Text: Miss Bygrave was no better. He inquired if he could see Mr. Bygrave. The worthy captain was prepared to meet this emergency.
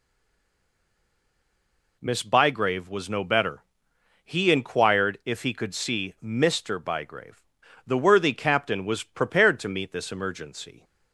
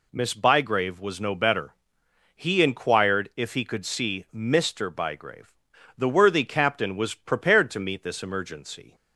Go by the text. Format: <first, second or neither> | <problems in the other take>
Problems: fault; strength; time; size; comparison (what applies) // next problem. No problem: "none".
second | stays silent before the first word; noticeable; until 1.9 s; 1.9 s long